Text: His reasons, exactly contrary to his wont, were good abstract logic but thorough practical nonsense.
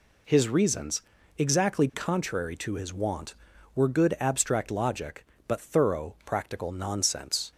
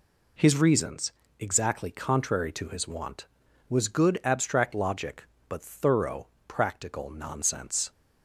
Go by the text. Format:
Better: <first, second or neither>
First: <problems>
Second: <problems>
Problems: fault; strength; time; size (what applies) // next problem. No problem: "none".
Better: first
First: none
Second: says "was" for "were"; at 3.6 s // pauses between "thorough" and "practical"; slight; at 6.2 s; 0.22 s long